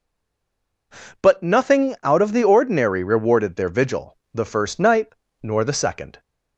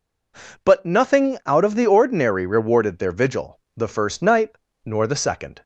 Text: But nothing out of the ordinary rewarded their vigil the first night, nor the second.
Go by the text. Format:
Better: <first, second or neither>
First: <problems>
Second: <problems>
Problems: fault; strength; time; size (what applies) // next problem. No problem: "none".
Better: second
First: stays silent before the first word; slight; until 0.9 s; 0.9 s long // pauses between "vigil" and "the"; slight; at 4.1 s; 0.16 s long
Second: pauses between "vigil" and "the"; slight; at 3.5 s; 0.16 s long